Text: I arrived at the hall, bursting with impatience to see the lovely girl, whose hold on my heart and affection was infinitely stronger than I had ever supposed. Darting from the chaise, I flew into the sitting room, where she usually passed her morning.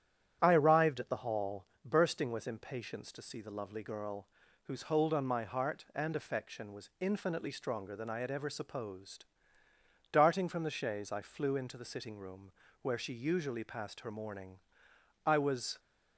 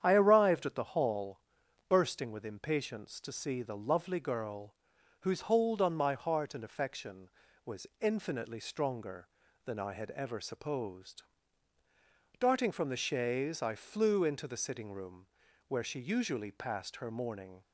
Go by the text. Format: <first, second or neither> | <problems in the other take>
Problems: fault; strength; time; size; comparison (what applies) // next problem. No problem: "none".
second | starts louder than the rest; strong; until 1.4 s; 10 dB; strong in the second // goes on to say "I was"; from 15.2 s on; 0.54 s long